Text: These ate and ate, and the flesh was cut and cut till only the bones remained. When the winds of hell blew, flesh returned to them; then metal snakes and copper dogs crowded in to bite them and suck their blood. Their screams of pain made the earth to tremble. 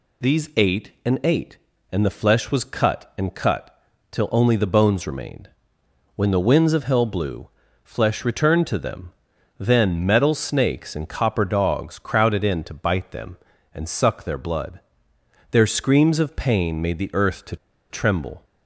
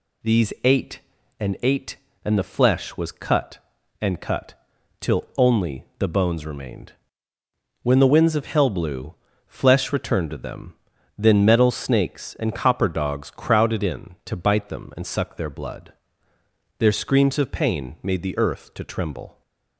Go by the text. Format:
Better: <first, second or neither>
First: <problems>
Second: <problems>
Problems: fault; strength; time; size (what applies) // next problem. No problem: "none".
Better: second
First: pauses between "cut" and "till"; slight; at 3.7 s; 0.36 s long // pauses between "to" and "tremble"; slight; at 17.5 s; 0.34 s long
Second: pauses between "cut" and "till"; at 4.5 s; 0.44 s long